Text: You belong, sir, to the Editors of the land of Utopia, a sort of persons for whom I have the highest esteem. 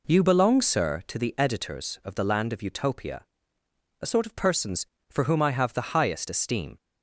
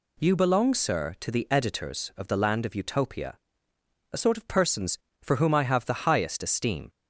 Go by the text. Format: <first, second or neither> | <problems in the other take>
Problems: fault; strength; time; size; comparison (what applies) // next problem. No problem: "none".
second | starts louder than the rest; until 1.2 s; 3.5 dB